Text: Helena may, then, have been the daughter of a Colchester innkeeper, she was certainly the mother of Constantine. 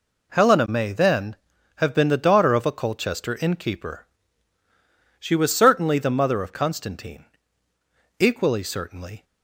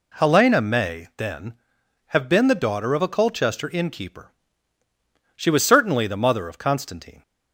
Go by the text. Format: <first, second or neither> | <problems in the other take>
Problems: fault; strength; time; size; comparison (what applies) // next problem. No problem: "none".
second | goes on to say "Equally certainly"; noticeable; from 8.1 s on; 1.0 s long